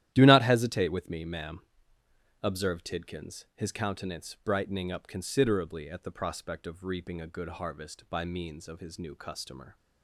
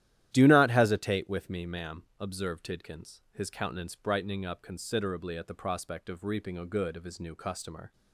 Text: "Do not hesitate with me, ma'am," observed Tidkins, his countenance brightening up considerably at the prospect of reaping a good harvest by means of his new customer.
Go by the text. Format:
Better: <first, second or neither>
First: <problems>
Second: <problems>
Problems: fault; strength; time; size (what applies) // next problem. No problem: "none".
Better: first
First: starts louder than the rest; strong; until 1.1 s; 12.5 dB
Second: starts louder than the rest; strong; until 1.3 s; 12.5 dB // skips "harvest by means"; at 6.9 s